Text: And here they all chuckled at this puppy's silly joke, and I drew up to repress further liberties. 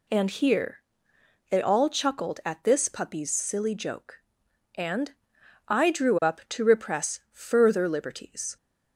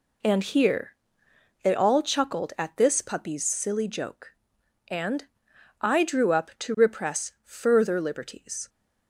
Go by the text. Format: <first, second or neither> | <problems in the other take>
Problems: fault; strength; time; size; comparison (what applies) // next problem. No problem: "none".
first | gets quieter; throughout; 6.5 dB // pauses between "here" and "they"; noticeable; at 0.9 s; 0.68 s long; noticeable in the first // pauses between "and" and "I"; noticeable; at 5.2 s; 0.54 s long; noticeable in the first